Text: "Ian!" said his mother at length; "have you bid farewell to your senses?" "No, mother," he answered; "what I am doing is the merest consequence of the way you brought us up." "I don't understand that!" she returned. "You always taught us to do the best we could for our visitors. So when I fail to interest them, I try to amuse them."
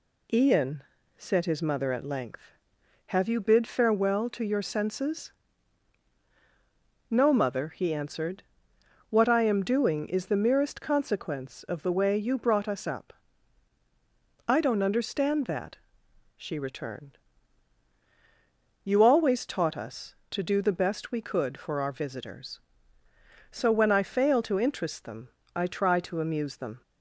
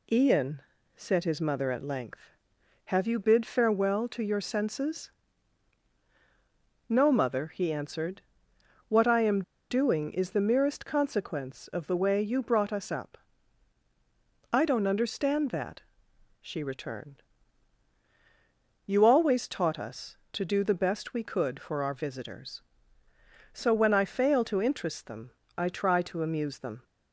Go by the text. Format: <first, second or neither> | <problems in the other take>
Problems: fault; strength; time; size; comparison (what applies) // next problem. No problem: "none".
first | pauses between "am" and "doing"; slight; at 9.4 s; 0.28 s long